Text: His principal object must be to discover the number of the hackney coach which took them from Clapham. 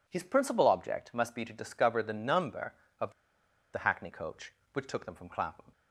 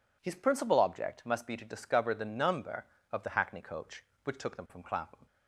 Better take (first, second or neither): second